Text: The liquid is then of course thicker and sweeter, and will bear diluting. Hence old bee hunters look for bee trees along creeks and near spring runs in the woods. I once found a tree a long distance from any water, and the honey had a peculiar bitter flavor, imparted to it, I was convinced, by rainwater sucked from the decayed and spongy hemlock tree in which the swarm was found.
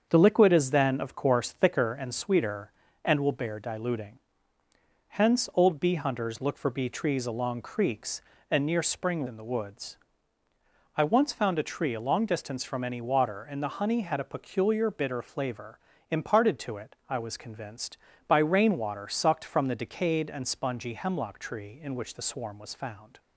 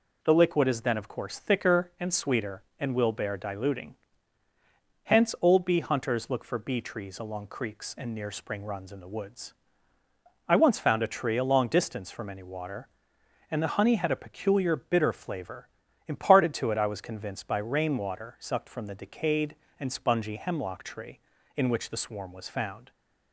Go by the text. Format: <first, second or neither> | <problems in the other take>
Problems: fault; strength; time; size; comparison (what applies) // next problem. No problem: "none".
second | starts louder than the rest; until 1.1 s; 7 dB // skips "runs"; at 9.2 s